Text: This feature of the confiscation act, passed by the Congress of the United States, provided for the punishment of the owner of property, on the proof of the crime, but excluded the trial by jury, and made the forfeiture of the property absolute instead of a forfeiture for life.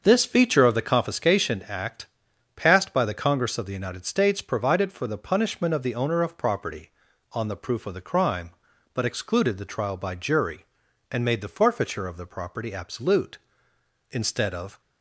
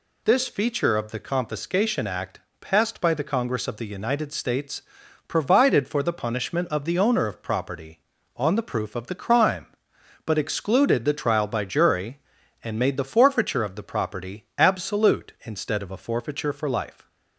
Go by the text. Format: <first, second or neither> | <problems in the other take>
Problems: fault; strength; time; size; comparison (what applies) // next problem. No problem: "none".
second | starts louder than the rest; until 1.0 s; 6.5 dB // stops before "a forfeiture for life"; at 14.7 s